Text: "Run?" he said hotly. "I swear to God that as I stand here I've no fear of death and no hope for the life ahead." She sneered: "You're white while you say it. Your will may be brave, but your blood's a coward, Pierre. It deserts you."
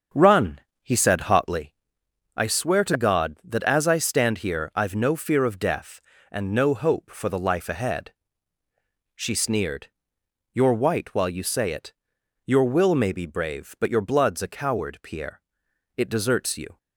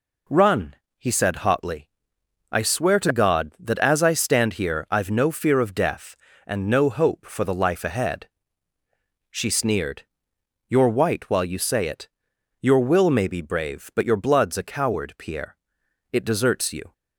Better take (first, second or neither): second